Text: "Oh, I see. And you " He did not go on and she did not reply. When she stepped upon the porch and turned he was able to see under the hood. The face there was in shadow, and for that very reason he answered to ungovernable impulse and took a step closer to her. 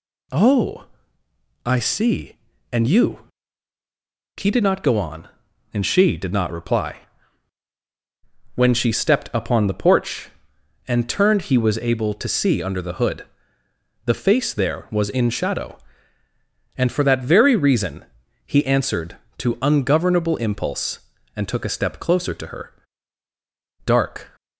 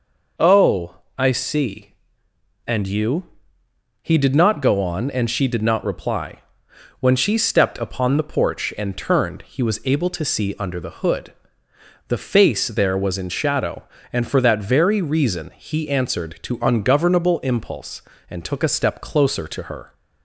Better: second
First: pauses between "reason" and "he"; at 18.0 s; 0.40 s long // goes on to say "Dark"; from 23.8 s on; 0.50 s long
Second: none

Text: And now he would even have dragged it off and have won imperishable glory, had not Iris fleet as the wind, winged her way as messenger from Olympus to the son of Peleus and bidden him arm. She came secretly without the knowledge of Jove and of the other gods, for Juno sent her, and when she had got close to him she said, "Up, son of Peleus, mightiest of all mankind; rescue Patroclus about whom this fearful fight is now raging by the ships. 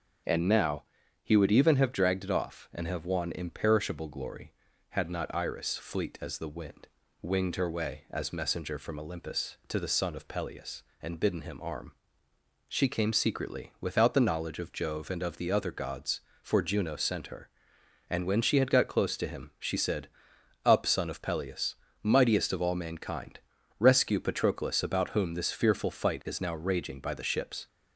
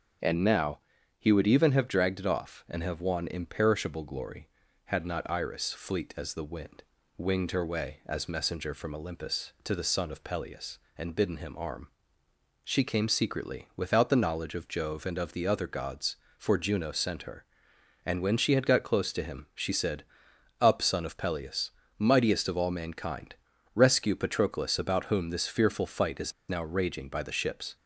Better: first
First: starts louder than the rest; noticeable; until 1.6 s; 6 dB // pauses between "now" and "he"; at 0.8 s; 0.38 s long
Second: starts louder than the rest; noticeable; until 1.6 s; 6 dB // pauses between "now" and "he"; at 0.7 s; 0.38 s long // pauses between "is" and "now"; slight; at 26.3 s; 0.17 s long

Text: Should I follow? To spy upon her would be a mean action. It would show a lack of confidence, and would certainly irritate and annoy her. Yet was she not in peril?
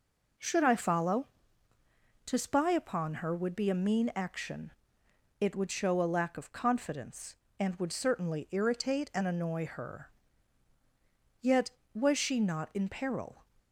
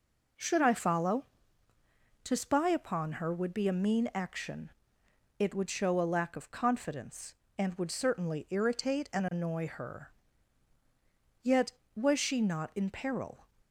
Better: neither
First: none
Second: none

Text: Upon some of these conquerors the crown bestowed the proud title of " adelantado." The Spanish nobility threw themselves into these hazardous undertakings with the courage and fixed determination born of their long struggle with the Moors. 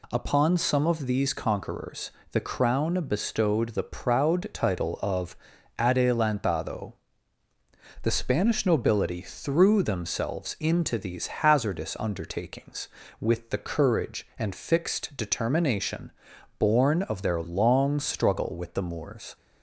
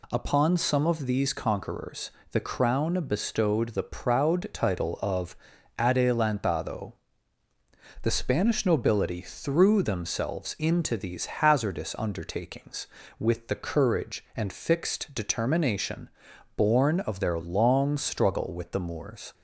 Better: neither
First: pauses between "conquerors" and "the"; slight; at 2.1 s; 0.22 s long // pauses between "determination" and "born"; noticeable; at 16.1 s; 0.46 s long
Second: pauses between "conquerors" and "the"; slight; at 2.1 s; 0.22 s long // pauses between "determination" and "born"; noticeable; at 16.0 s; 0.46 s long

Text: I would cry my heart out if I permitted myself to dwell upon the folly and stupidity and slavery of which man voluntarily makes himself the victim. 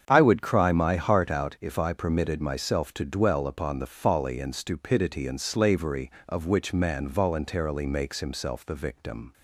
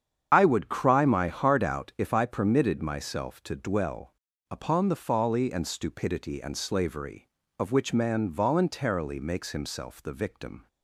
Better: first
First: starts louder than the rest; strong; until 1.0 s; 7.5 dB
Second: loses the start of "I"; at 0.3 s; 40 ms // starts louder than the rest; strong; until 1.3 s; 8 dB // pauses between "dwell" and "upon"; at 4.1 s; 0.38 s long

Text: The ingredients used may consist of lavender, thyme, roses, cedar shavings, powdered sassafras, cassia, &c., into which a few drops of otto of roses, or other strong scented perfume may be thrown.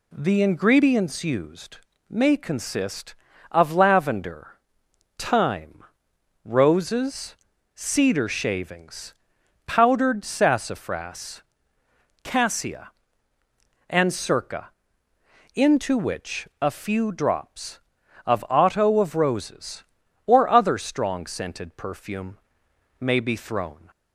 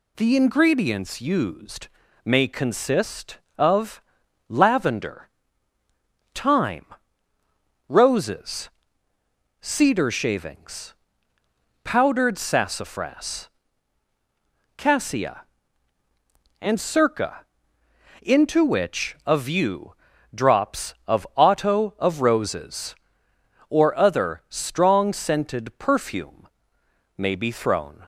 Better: first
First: pauses between "used" and "may"; slight; at 1.7 s; 0.32 s long // pauses between "perfume" and "may"; noticeable; at 22.3 s; 0.64 s long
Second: pauses between "used" and "may"; slight; at 1.8 s; 0.34 s long // pauses between "of" and "lavender"; noticeable; at 4.0 s; 0.46 s long // says "view" for "few"; at 19.3 s // pauses between "perfume" and "may"; noticeable; at 26.4 s; 0.70 s long

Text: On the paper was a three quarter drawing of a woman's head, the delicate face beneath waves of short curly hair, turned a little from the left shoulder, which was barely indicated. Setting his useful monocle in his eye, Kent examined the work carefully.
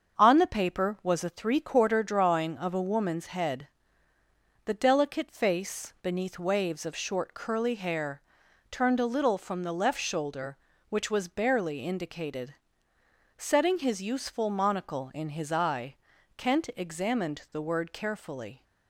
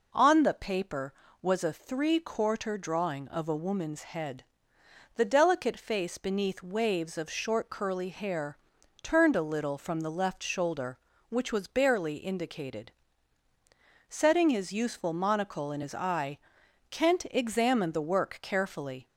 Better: second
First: starts louder than the rest; until 1.2 s; 7 dB // says "word" for "work"; at 17.6 s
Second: none

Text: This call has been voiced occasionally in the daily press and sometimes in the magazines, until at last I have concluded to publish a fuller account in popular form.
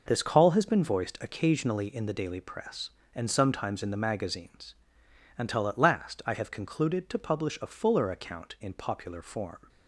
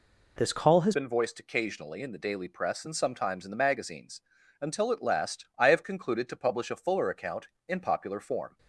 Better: first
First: none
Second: changes voice at "been"; from 0.9 s on; 7.6 s long

